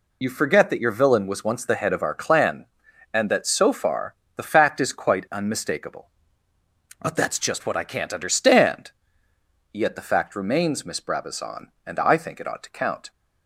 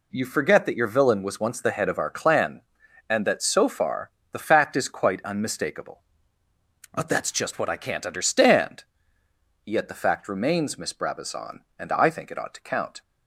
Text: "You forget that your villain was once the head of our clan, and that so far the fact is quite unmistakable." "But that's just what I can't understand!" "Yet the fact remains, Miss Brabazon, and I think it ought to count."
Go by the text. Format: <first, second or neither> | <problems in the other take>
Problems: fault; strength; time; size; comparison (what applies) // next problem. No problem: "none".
second | loses the start of "You"; at 0.2 s; 60 ms // pauses between "far" and "the"; slight; at 4.1 s; 0.22 s long; slight in the second